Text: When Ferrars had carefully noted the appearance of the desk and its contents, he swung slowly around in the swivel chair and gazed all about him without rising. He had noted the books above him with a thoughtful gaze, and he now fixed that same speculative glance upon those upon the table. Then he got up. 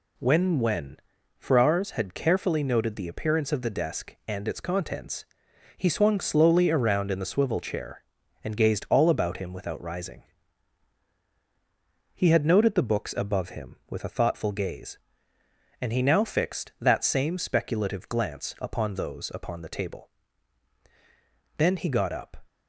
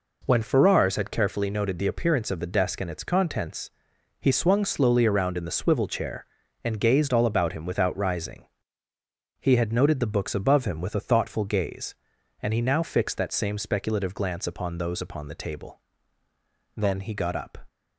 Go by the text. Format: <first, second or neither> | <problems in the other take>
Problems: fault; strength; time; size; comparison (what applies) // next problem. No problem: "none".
second | says "When" twice; at 0.5 s